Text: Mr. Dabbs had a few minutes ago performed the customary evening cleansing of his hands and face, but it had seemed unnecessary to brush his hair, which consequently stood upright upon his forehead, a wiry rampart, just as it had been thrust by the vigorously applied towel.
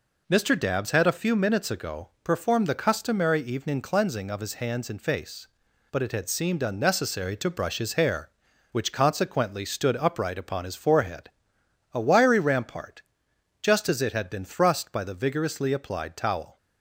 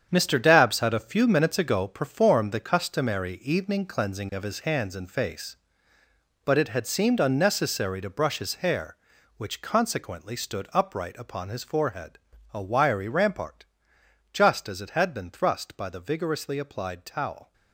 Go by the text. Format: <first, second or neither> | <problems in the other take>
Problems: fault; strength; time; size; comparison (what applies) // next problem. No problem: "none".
first | gets quieter; strong; throughout; 10 dB